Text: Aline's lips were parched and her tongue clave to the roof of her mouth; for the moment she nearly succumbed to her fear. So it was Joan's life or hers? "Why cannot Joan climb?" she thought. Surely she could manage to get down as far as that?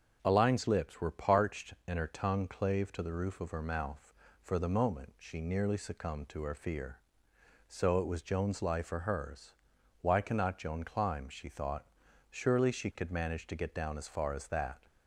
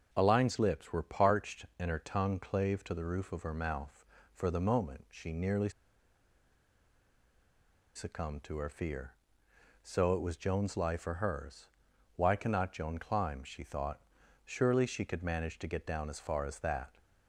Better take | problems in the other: first | starts louder than the rest; until 1.1 s; 6.5 dB; also in the first // pauses between "nearly" and "succumbed"; strong; at 5.6 s; 2.2 s long

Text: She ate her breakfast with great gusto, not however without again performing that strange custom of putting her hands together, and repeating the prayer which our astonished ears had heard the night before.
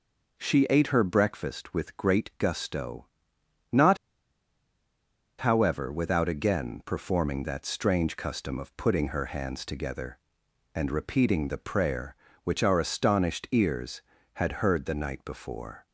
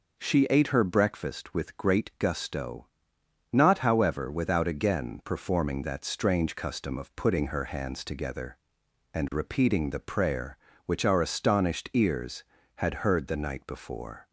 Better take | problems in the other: second | pauses between "not" and "however"; strong; at 3.9 s; 1.4 s long

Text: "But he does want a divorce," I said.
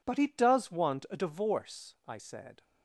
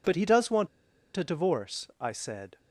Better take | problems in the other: first | pauses between "want" and "a"; noticeable; at 0.6 s; 0.48 s long

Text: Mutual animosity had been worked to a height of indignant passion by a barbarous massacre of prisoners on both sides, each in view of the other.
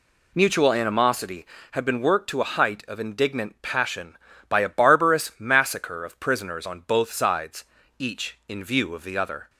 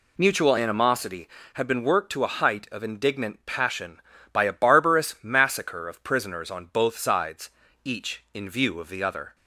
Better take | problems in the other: neither | none

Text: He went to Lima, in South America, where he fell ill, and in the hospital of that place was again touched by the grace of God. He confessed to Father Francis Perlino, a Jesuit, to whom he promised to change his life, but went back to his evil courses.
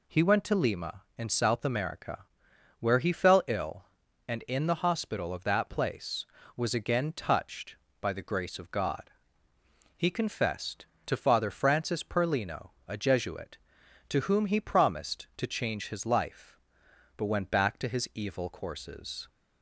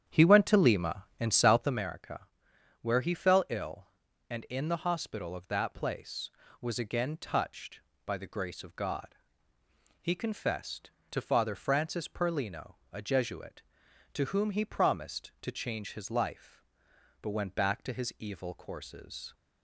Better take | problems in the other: first | starts louder than the rest; strong; until 1.9 s; 9 dB

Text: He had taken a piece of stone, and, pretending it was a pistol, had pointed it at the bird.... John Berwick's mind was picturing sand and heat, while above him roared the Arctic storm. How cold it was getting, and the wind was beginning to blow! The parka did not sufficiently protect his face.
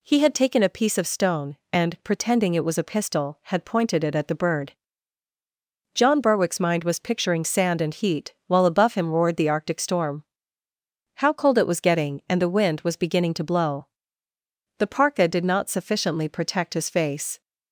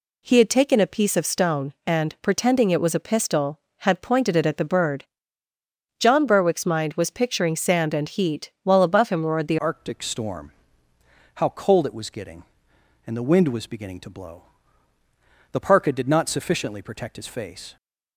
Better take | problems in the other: first | changes voice at "Arctic"; from 9.5 s on; 8.2 s long

